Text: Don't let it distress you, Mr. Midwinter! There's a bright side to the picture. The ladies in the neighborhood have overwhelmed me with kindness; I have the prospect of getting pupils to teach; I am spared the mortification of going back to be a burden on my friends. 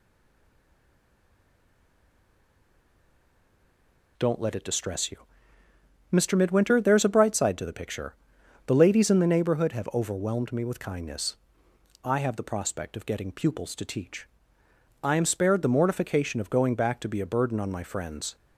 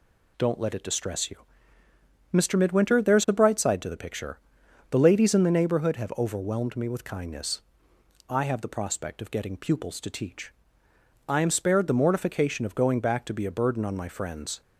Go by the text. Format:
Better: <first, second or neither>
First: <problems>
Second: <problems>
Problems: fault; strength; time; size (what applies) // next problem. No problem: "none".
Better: second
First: stays silent before the first word; strong; until 4.1 s; 4.1 s long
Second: none